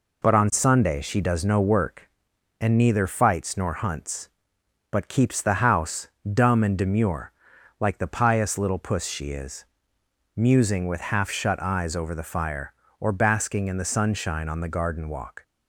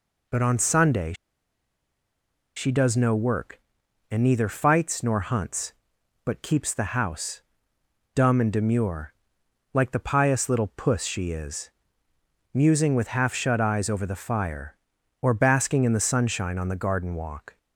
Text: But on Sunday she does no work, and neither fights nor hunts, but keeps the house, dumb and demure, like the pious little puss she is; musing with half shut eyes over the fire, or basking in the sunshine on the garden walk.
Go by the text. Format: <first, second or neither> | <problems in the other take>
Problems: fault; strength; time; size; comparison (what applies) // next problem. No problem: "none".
first | pauses between "Sunday" and "she"; strong; at 1.1 s; 1.4 s long